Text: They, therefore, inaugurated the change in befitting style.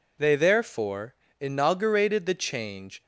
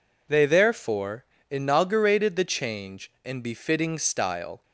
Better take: second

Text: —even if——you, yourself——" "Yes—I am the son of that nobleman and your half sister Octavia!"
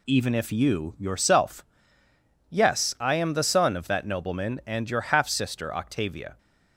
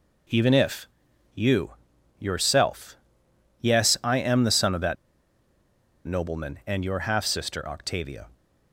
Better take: first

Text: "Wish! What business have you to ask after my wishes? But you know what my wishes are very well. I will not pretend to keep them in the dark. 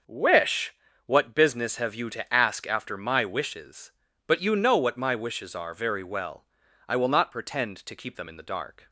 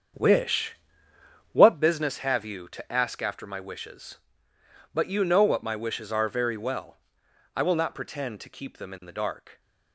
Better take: first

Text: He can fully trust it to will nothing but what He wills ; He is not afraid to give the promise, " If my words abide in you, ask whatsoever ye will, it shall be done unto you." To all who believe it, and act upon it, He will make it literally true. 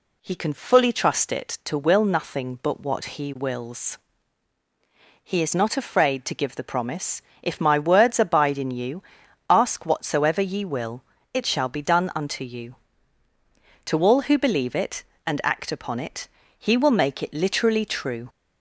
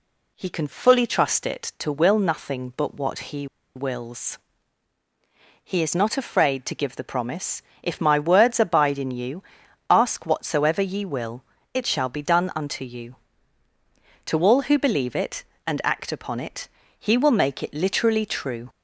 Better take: first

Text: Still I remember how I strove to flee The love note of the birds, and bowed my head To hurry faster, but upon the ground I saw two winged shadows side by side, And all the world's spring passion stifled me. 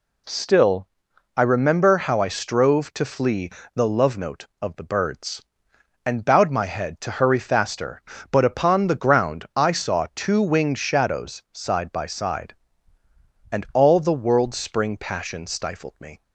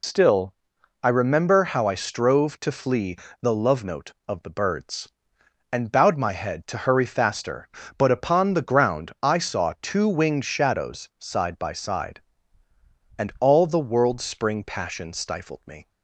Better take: first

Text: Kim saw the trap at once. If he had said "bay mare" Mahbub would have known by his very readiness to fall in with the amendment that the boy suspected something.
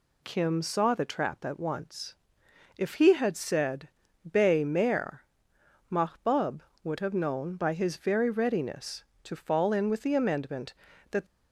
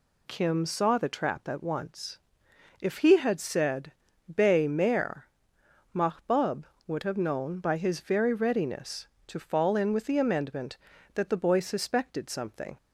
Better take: second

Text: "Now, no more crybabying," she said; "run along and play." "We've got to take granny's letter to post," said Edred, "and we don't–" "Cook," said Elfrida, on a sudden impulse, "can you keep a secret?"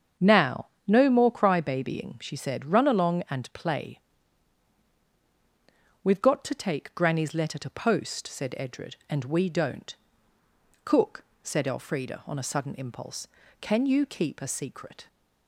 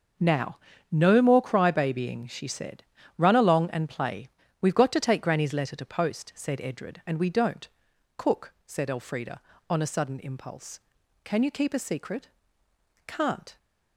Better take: first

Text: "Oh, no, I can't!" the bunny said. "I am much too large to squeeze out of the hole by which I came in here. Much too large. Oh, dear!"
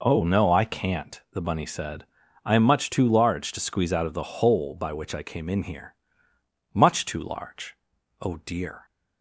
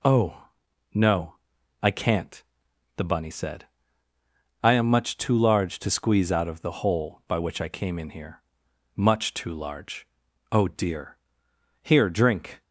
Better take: first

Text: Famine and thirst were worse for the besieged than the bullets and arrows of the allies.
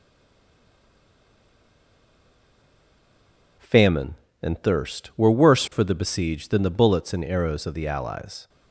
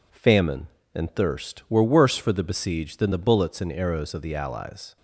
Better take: second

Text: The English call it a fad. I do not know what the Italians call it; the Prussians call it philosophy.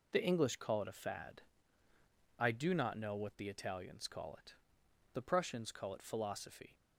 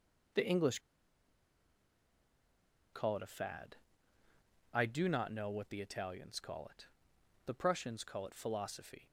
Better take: first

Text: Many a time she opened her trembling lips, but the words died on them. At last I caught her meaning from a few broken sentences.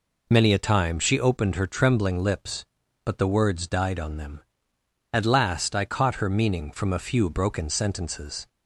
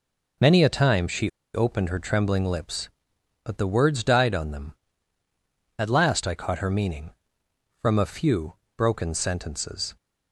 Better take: first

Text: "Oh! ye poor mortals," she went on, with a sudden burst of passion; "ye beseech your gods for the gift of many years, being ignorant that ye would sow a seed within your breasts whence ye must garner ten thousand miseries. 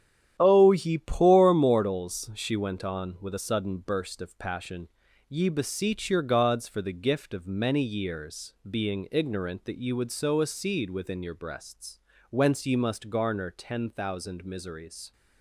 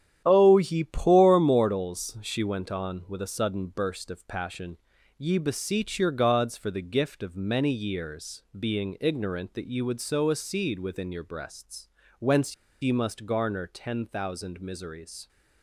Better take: first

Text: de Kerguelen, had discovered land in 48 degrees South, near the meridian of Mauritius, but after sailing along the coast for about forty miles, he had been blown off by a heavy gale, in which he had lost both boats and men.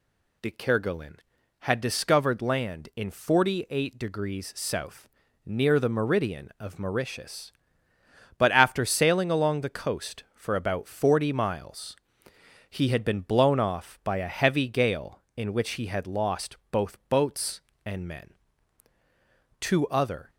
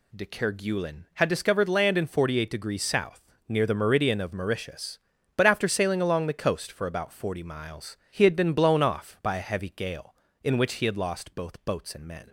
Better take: second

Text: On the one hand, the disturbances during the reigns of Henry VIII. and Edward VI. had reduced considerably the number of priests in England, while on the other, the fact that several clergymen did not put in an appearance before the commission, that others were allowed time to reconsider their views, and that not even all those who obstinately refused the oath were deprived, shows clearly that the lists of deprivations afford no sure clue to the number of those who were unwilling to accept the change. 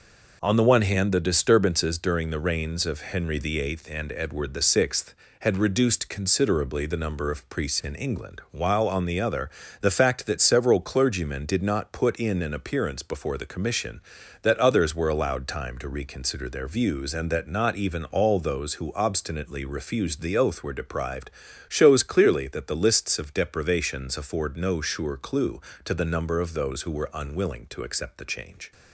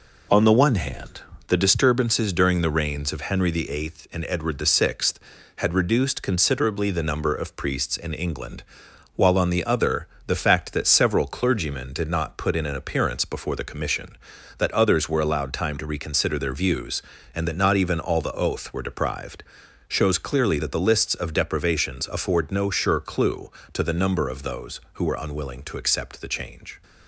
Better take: first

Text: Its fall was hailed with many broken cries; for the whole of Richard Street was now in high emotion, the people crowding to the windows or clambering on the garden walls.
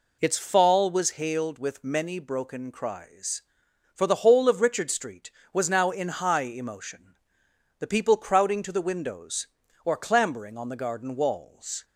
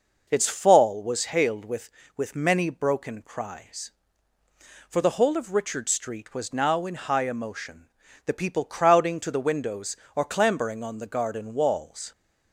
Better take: first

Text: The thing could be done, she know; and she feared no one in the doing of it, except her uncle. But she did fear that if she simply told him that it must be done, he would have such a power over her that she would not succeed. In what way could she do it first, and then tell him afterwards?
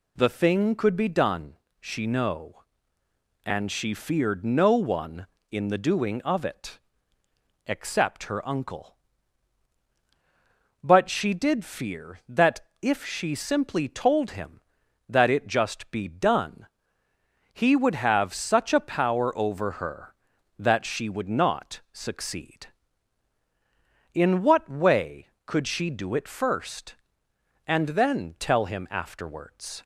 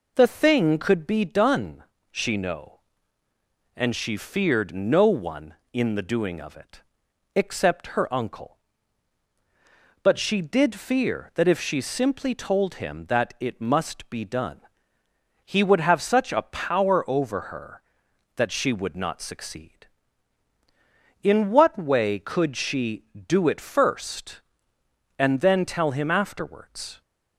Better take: second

